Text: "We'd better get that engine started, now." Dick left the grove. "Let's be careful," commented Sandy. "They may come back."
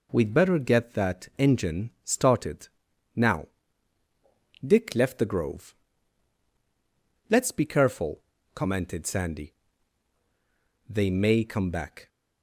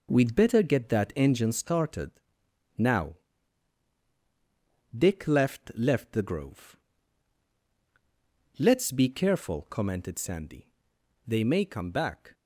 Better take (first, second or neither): first